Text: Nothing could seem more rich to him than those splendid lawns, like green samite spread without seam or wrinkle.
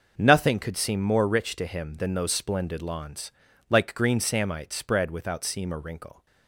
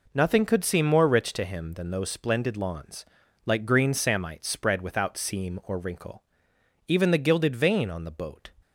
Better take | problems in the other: first | goes on to say "Even the gilded vane on the boat"; from 6.8 s on; 1.6 s long

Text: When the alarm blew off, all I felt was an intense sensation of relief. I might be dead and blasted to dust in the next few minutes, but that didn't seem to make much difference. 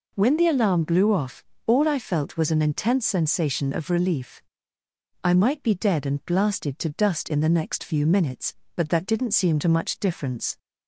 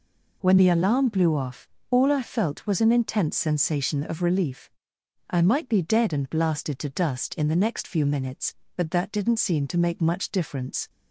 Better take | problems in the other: second | skips "make"; at 9.6 s

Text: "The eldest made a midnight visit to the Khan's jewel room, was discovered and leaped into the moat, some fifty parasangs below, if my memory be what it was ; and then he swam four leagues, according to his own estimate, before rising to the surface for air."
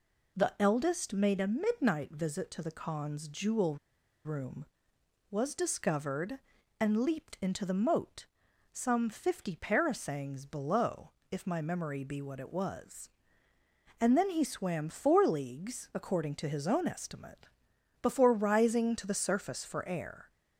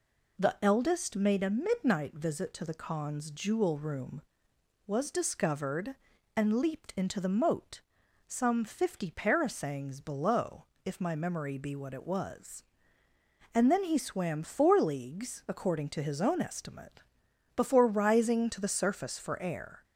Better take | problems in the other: second | pauses between "jewel" and "room"; noticeable; at 3.7 s; 0.47 s long

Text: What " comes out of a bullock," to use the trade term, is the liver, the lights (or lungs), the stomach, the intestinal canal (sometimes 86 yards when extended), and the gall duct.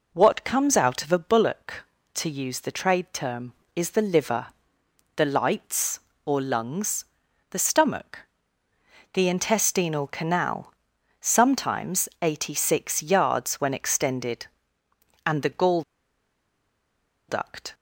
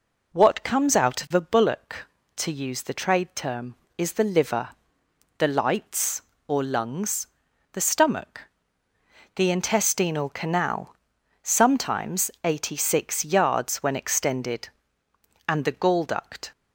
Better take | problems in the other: second | pauses between "gall" and "duct"; strong; at 15.8 s; 1.4 s long

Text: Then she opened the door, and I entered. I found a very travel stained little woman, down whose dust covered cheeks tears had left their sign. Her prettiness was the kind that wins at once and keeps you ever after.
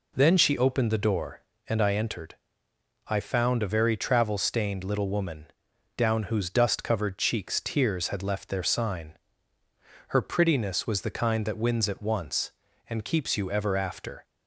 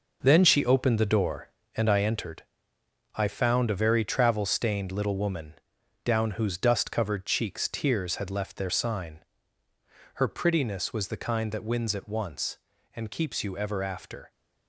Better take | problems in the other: first | gets quieter; strong; throughout; 8.5 dB

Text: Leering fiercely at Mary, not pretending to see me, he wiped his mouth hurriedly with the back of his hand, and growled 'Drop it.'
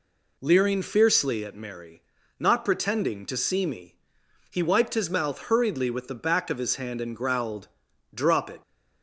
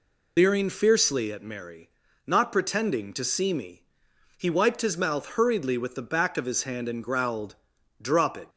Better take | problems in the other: first | loses the start of "Leering"; at 0.3 s; 100 ms // pauses between "growled" and "Drop"; noticeable; at 7.5 s; 0.46 s long; noticeable in the first

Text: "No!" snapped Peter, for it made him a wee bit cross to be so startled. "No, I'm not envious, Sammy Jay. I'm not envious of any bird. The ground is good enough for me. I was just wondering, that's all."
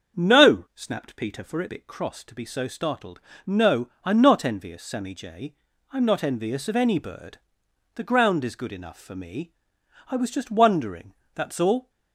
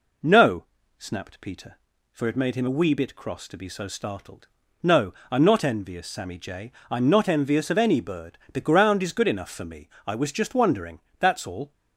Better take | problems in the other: second | starts louder than the rest; until 1.2 s; 7 dB // skips "made him a wee"; at 1.6 s

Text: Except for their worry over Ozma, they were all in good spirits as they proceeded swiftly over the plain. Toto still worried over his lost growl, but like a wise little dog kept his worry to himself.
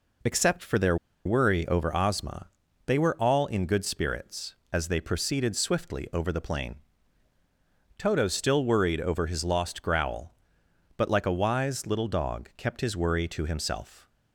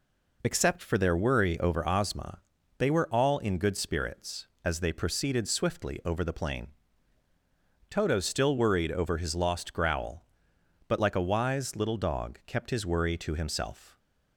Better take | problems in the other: second | pauses between "their" and "worry"; slight; at 0.9 s; 0.29 s long

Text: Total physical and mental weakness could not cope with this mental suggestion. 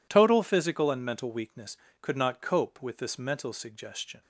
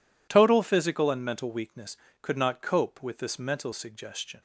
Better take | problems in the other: neither | none

